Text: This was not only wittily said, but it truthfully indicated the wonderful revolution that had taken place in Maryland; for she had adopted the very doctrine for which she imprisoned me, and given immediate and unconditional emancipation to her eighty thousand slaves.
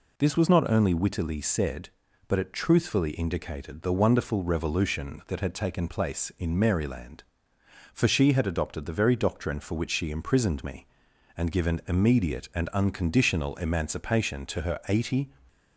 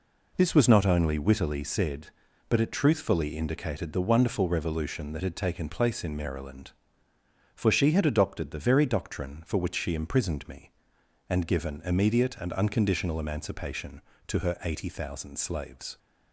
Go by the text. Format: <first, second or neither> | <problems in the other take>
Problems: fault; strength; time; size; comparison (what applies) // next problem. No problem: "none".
second | stops before "thousand slaves"; at 15.4 s